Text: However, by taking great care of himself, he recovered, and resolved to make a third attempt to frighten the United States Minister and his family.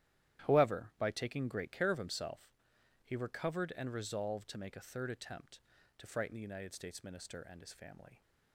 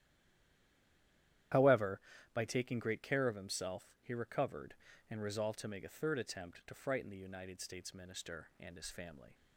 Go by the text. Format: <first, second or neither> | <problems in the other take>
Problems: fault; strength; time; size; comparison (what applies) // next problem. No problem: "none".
first | stays silent before the first word; noticeable; until 1.5 s; 1.5 s long // starts louder than the rest; strong; until 2.8 s; 12 dB; strong in the first